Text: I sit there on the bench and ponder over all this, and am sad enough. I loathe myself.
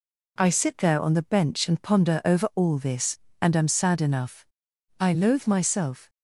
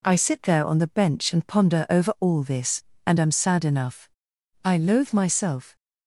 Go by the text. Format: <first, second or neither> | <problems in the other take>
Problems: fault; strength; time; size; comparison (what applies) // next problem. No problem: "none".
neither | none